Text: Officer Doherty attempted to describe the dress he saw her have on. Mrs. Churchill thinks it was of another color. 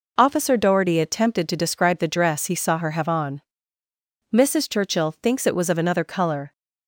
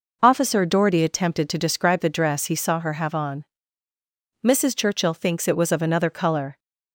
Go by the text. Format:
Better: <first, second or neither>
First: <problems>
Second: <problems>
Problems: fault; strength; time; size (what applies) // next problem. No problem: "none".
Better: neither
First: none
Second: none